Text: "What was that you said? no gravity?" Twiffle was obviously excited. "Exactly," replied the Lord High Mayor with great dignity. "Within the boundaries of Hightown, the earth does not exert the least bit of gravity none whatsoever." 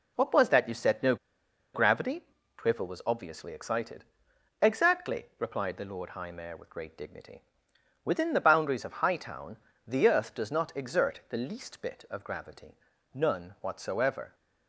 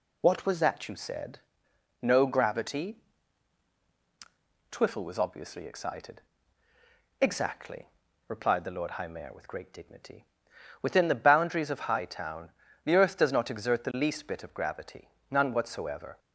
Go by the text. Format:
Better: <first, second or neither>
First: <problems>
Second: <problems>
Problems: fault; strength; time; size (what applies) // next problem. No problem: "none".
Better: second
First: pauses between "no" and "gravity"; noticeable; at 1.1 s; 0.58 s long // pauses between "gravity" and "none"; slight; at 12.7 s; 0.36 s long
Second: pauses between "gravity" and "none"; slight; at 15.0 s; 0.22 s long